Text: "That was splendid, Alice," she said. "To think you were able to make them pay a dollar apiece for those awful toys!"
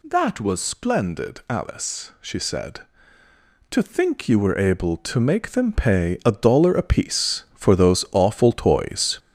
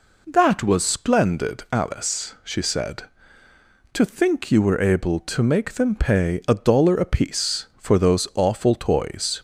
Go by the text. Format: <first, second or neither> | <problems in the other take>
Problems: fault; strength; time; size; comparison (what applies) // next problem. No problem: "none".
second | gets louder; throughout; 6 dB